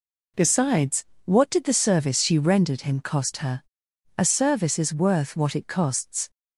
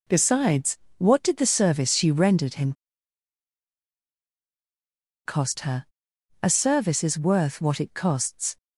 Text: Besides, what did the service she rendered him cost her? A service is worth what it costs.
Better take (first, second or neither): first